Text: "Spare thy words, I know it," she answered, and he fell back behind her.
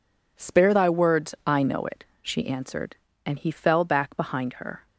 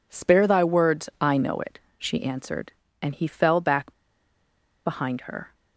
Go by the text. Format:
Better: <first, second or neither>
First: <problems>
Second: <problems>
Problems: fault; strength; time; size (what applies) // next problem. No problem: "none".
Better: first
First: none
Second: pauses between "back" and "behind"; noticeable; at 3.9 s; 0.92 s long